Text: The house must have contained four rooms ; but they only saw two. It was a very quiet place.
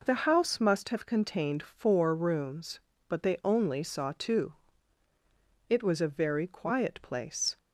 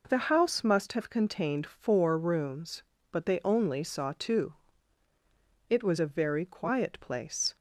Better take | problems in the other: neither | none

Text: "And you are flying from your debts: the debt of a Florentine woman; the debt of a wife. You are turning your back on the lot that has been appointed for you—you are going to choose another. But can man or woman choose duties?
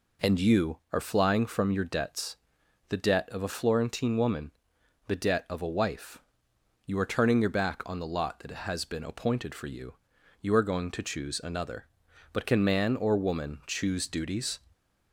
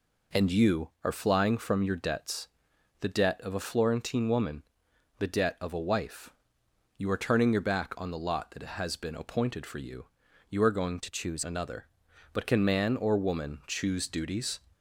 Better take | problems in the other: first | changes voice from "to" to "choose"; from 10.9 to 11.4 s; 0.5 s long

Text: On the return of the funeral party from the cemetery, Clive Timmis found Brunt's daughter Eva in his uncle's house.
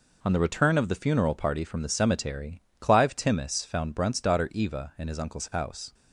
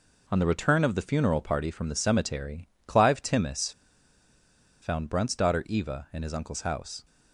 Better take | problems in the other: first | pauses between "Timmis" and "found"; at 3.7 s; 1.1 s long

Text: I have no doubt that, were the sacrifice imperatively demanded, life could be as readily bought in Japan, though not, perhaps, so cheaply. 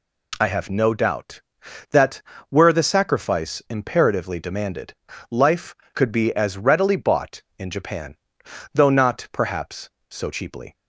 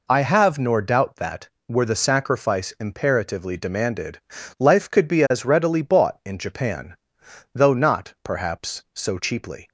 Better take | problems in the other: first | says "nor" for "no"; at 0.5 s

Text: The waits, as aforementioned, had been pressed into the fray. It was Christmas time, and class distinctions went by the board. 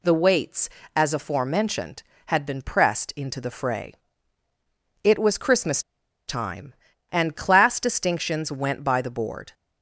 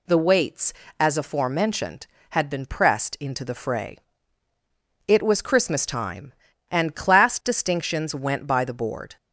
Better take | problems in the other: second | pauses between "Christmas" and "time"; noticeable; at 5.8 s; 0.47 s long

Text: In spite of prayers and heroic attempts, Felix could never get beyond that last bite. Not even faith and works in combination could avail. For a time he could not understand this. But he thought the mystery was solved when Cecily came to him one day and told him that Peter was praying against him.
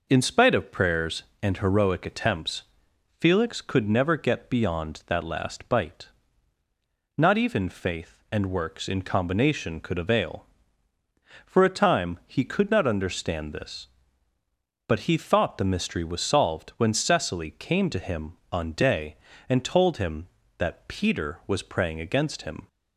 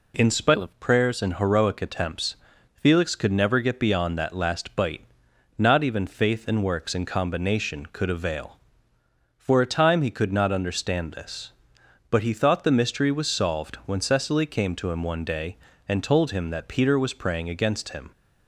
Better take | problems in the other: second | says "on" for "one"; at 18.4 s

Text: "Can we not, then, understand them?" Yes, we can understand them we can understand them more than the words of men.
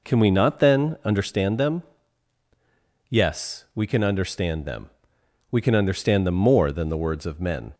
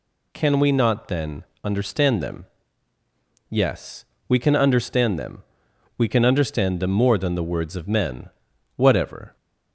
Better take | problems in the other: first | pauses between "them" and "we"; noticeable; at 5.4 s; 0.56 s long; noticeable in the first // goes on to say "Whatever"; from 8.7 s on; 0.60 s long

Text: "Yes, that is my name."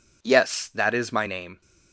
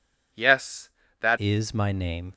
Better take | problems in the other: first | changes voice at "is"; from 1.3 s on; 1.0 s long

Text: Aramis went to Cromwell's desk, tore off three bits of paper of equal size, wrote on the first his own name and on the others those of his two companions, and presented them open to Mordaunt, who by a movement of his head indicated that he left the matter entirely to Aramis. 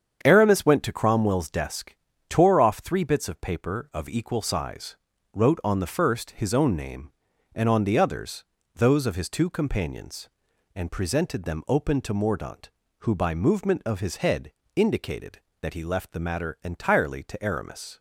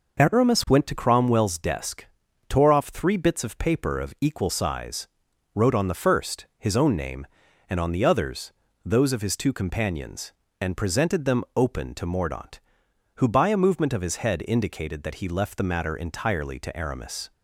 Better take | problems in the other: second | starts louder than the rest; strong; until 1.2 s; 8 dB // pauses between "others" and "those"; slight; at 8.4 s; 0.32 s long; slight in the second // skips "a"; at 13.3 s // pauses between "head" and "indicated"; slight; at 14.5 s; 0.24 s long

